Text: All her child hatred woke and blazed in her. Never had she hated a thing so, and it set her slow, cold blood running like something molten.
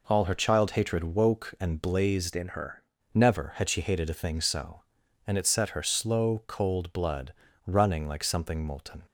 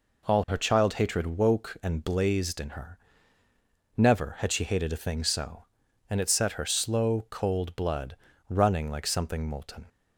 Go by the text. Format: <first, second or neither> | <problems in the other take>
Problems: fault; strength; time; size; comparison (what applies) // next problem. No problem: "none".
second | changes voice from "in" to "her"; from 2.3 to 2.8 s; 0.5 s long // pauses between "blood" and "running"; slight; at 7.3 s; 0.34 s long; slight in the second